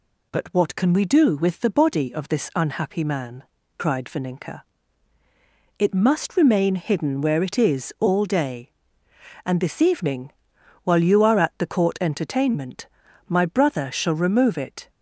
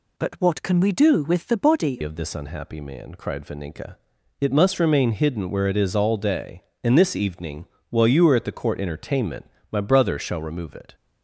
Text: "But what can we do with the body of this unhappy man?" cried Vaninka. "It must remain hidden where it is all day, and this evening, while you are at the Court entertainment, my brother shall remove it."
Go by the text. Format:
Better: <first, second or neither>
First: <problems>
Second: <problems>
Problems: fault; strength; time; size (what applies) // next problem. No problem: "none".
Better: first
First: none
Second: changes voice at "of"; from 2.0 s on; 8.9 s long